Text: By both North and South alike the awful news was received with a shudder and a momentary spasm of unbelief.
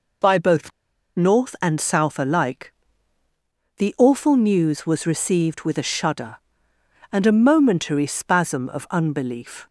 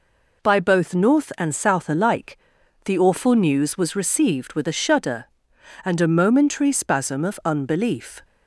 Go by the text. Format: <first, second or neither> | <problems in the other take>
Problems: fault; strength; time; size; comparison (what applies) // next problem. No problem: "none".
second | pauses between "both" and "North"; at 0.7 s; 0.45 s long // pauses between "alike" and "the"; at 2.7 s; 1.0 s long; noticeable in the second